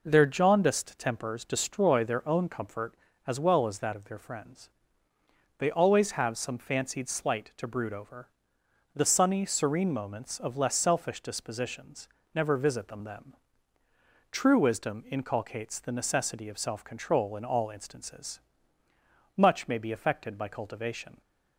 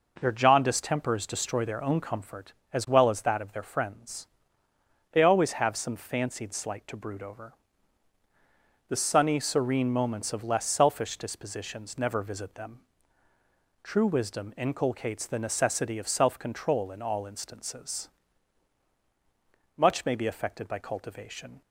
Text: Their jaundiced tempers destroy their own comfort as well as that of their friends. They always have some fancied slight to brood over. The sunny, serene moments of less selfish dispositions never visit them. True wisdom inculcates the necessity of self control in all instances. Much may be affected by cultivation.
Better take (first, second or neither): second